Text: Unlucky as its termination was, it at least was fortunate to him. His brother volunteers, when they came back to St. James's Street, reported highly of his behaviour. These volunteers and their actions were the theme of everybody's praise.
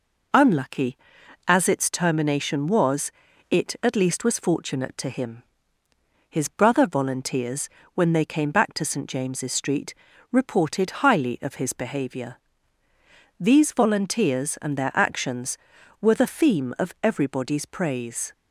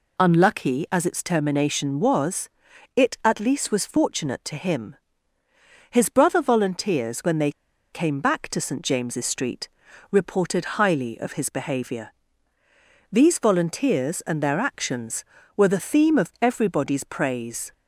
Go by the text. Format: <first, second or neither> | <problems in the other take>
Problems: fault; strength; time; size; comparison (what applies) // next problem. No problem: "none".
first | pauses between "they" and "came"; at 7.5 s; 0.40 s long